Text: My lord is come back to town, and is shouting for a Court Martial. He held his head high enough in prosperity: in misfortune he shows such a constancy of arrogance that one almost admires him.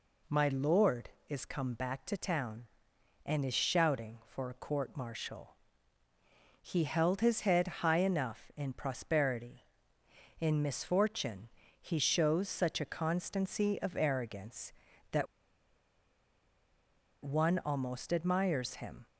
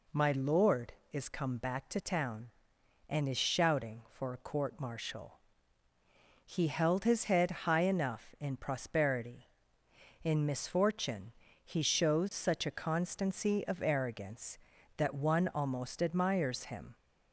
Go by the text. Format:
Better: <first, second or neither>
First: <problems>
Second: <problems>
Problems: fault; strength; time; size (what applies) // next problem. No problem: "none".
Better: second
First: pauses between "misfortune" and "he"; slight; at 11.4 s; 0.32 s long // pauses between "that" and "one"; strong; at 15.2 s; 1.9 s long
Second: pauses between "misfortune" and "he"; slight; at 11.3 s; 0.32 s long